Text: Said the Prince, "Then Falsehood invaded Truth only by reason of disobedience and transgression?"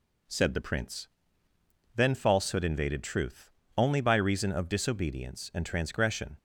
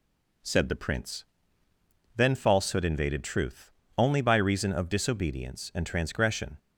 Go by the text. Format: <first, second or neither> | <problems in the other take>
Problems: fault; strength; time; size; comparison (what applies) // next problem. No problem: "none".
neither | pauses between "Truth" and "only"; slight; the same in both